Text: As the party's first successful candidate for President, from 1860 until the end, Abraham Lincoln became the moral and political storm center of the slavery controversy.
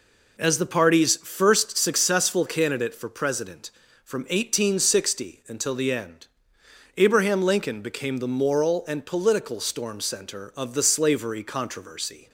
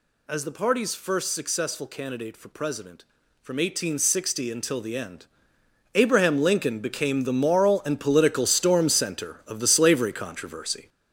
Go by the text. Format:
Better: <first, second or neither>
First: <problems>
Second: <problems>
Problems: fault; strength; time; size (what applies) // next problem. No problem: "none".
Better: first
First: none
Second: gets louder; noticeable; throughout; 6 dB